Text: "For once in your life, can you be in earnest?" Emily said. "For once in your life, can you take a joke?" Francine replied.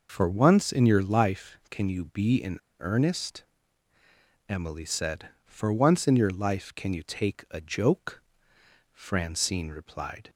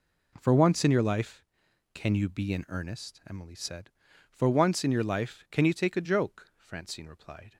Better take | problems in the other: second | pauses between "in" and "earnest"; slight; at 2.5 s; 0.23 s long

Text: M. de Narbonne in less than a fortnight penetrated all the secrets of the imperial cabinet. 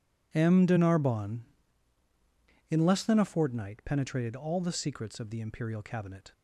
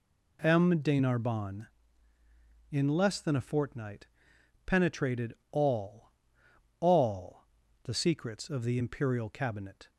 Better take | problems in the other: first | pauses between "fortnight" and "penetrated"; noticeable; at 4.0 s; 0.60 s long // pauses between "penetrated" and "all"; slight; at 5.3 s; 0.16 s long // says "all" twice; at 6.7 s

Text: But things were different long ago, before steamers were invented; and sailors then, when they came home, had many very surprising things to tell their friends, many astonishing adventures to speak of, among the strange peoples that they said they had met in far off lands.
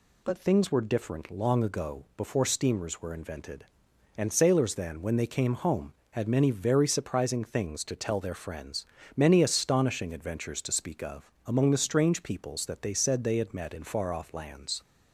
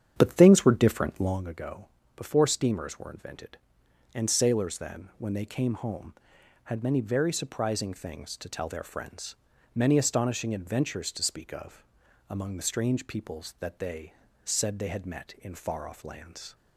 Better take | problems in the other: first | starts louder than the rest; strong; until 1.4 s; 9 dB // pauses between "they" and "said"; slight; at 14.1 s; 0.30 s long

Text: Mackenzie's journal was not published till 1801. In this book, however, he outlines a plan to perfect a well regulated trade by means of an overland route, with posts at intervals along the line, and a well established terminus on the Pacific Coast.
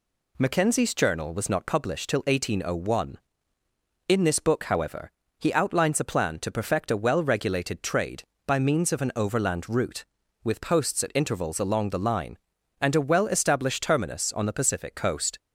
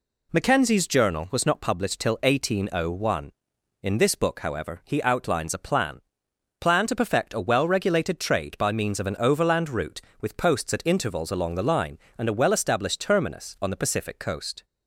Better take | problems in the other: first | says "plan" twice; at 6.6 s

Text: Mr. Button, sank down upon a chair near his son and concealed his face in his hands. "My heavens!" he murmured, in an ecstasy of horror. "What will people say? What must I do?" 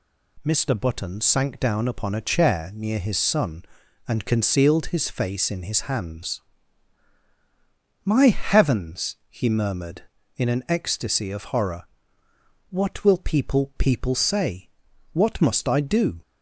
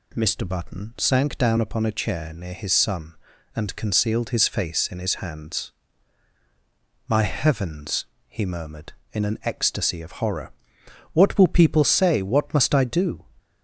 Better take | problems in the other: second | says "people" twice; at 13.7 s

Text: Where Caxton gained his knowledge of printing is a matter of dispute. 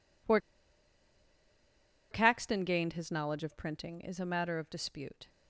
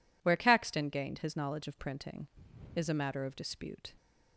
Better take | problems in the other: second | pauses between "Where" and "Caxton"; strong; at 0.3 s; 1.7 s long

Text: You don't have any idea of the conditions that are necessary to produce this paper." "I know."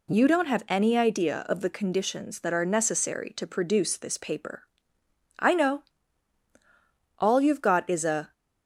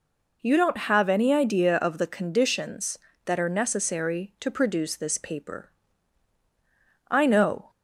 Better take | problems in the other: second | goes on to say "All you've got is a"; noticeable; from 7.1 s on; 1.1 s long

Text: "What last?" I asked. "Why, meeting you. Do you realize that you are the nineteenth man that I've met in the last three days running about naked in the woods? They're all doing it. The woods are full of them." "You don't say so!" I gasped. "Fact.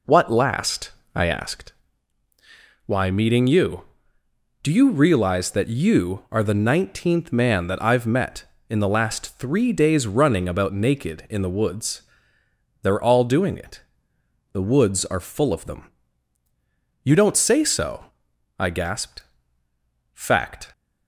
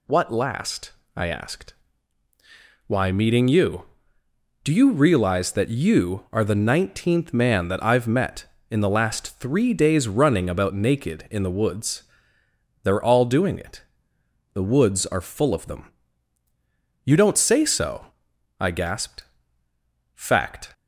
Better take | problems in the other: second | starts louder than the rest; noticeable; until 1.7 s; 4 dB

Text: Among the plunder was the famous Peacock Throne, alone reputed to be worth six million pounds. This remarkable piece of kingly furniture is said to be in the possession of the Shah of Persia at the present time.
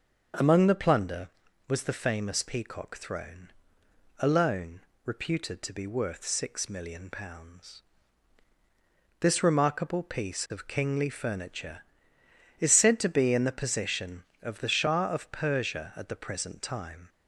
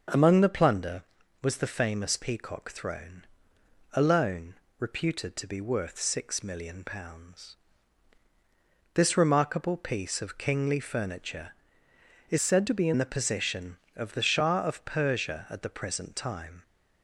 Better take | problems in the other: first | starts louder than the rest; until 1.5 s; 6 dB; also in the first // pauses between "alone" and "reputed"; slight; at 4.5 s; 0.24 s long; slight in the first // changes voice from "said" to "in"; from 12.4 to 12.9 s; 0.5 s long

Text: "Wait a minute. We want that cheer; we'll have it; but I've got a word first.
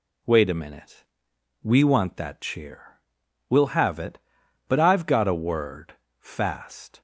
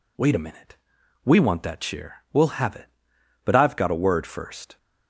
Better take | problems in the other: second | says "fast" for "first"; at 6.1 s

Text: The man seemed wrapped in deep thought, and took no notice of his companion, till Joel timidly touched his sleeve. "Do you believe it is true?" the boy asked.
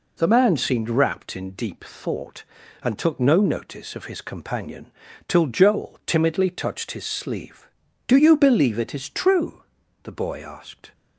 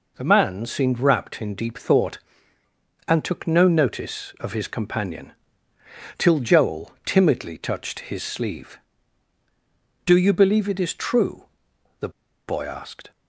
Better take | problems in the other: first | pauses between "the" and "boy"; at 12.0 s; 0.38 s long

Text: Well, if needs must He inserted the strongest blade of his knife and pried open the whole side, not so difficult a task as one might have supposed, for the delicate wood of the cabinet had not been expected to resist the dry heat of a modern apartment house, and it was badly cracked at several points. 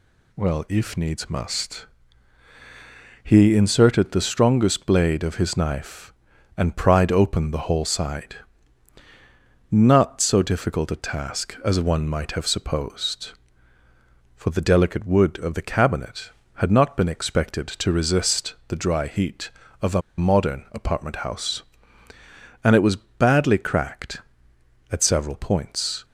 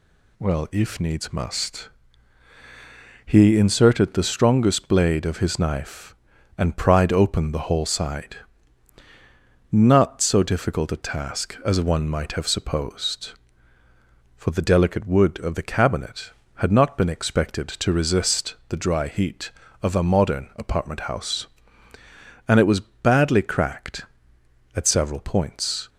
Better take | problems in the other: second | pauses between "must" and "He"; strong; at 1.8 s; 1.3 s long; strong in the second // pauses between "a" and "modern"; slight; at 20.0 s; 0.17 s long

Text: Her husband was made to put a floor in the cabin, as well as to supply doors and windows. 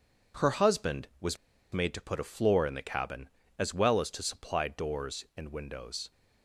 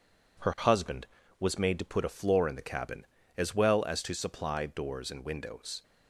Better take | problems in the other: second | pauses between "was" and "made"; slight; at 1.3 s; 0.35 s long

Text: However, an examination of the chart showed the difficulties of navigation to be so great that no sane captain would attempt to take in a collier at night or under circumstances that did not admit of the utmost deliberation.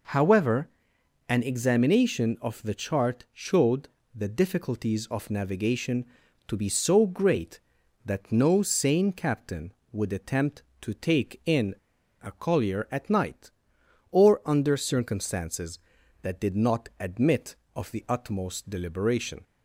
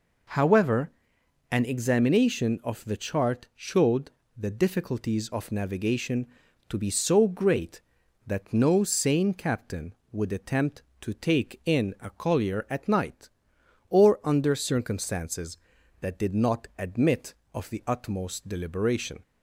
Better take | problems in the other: second | pauses between "showed" and "the"; slight; at 3.8 s; 0.26 s long; slight in the second // pauses between "in" and "a"; noticeable; at 11.7 s; 0.49 s long

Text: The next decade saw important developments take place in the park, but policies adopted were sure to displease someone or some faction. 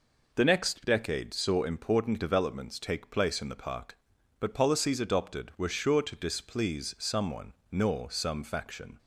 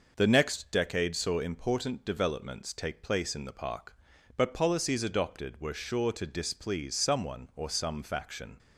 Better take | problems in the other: second | says "nor" for "or"; at 7.6 s

